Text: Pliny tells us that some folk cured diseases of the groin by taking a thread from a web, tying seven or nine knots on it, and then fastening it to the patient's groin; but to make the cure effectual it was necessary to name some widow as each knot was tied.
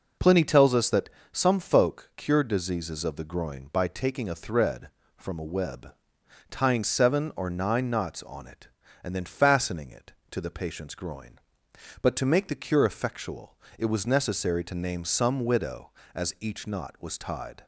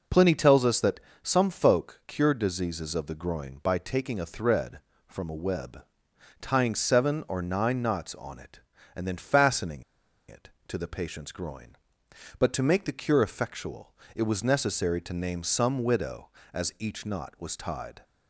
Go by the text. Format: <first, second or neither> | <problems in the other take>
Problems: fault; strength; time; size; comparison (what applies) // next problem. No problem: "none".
first | pauses between "that" and "some"; slight; at 1.0 s; 0.22 s long; slight in the first // pauses between "fastening" and "it"; noticeable; at 9.8 s; 0.46 s long // pauses between "effectual" and "it"; slight; at 13.9 s; 0.18 s long; slight in the first